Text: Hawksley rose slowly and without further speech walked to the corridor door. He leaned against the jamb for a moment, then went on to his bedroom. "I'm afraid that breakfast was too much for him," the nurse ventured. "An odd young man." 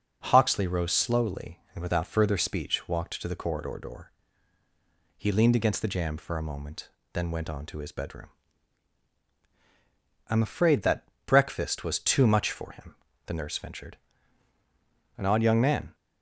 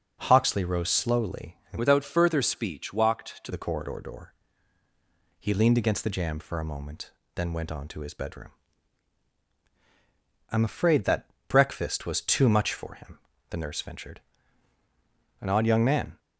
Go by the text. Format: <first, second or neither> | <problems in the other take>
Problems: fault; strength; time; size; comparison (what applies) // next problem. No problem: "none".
first | changes voice from "without" to "to"; from 1.7 to 3.5 s; 1.8 s long // pauses between "that" and "breakfast"; slight; at 11.2 s; 0.20 s long; slight in the first